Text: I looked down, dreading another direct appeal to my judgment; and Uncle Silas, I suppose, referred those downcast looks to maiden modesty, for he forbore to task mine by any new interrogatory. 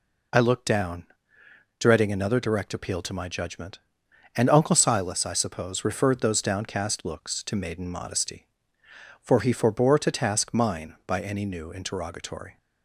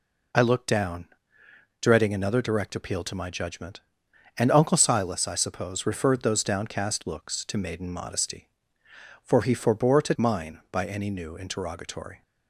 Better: first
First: none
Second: skips "task"; at 10.1 s

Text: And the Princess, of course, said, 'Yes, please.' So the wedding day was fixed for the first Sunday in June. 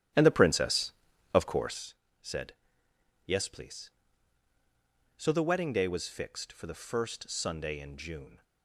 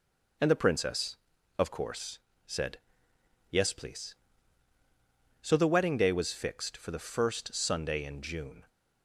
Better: second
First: starts louder than the rest; strong; until 1.8 s; 12 dB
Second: none

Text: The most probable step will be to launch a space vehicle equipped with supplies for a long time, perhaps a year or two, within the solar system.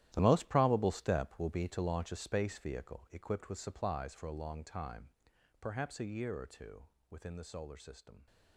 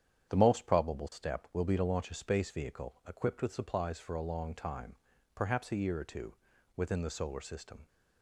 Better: second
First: gets quieter; strong; throughout; 14.5 dB // starts louder than the rest; strong; until 1.1 s; 13 dB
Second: starts louder than the rest; strong; until 1.3 s; 9 dB

